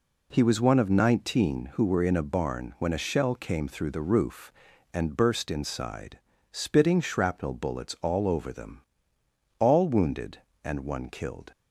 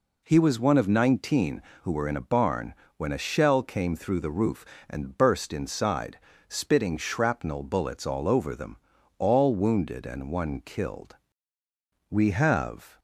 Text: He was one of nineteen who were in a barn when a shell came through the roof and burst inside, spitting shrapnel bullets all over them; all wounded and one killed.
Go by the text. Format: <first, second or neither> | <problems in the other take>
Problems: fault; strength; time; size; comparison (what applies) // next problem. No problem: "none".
first | pauses between "barn" and "when"; slight; at 2.7 s; 0.22 s long // goes on to say "We have"; noticeable; from 12.0 s on; 0.90 s long